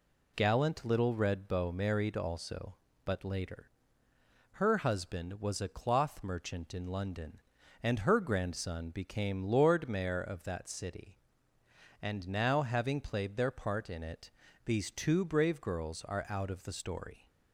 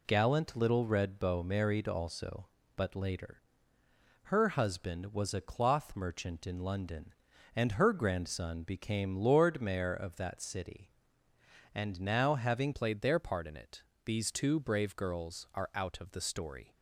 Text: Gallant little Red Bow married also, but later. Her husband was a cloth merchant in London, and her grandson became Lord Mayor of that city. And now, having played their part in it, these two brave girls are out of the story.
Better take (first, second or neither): first